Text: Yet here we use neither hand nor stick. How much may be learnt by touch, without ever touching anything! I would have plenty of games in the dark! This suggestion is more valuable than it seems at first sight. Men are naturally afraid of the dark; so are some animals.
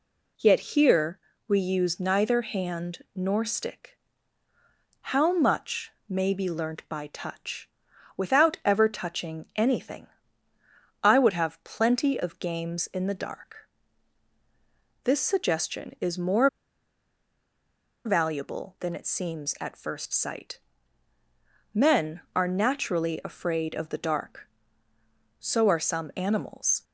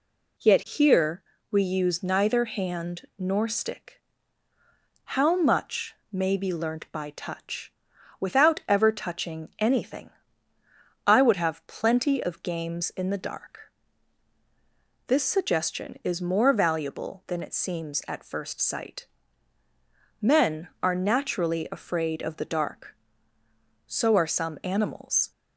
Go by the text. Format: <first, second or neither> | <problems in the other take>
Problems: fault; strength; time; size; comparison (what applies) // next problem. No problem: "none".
second | pauses between "here" and "we"; slight; at 1.1 s; 0.28 s long; slight in the second // pauses between "much" and "may"; slight; at 5.9 s; 0.18 s long; slight in the second // pauses between "more" and "valuable"; strong; at 16.4 s; 1.5 s long